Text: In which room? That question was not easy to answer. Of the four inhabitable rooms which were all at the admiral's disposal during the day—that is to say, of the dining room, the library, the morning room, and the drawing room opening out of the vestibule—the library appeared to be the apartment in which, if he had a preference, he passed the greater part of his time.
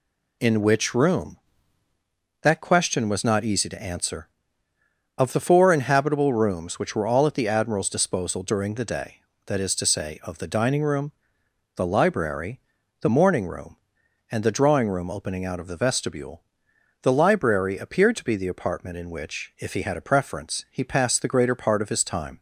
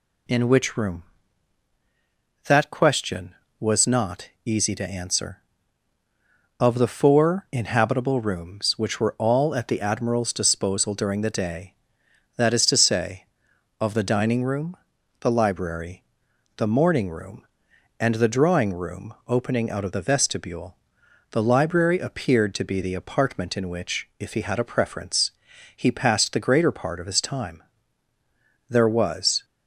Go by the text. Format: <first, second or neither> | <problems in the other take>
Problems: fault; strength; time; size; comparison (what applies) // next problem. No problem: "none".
first | pauses between "not" and "easy"; slight; at 4.2 s; 0.16 s long // pauses between "room" and "opening"; slight; at 19.1 s; 0.16 s long // goes on to say "There was"; noticeable; from 28.6 s on; 0.76 s long